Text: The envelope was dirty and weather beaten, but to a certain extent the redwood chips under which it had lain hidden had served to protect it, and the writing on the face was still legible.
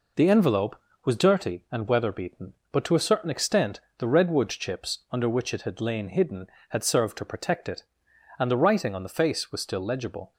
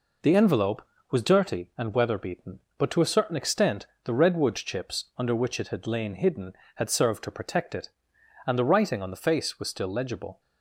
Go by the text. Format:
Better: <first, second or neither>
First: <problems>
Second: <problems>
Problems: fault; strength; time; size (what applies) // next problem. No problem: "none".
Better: neither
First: pauses between "extent" and "the"; slight; at 3.7 s; 0.18 s long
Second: pauses between "extent" and "the"; slight; at 3.8 s; 0.18 s long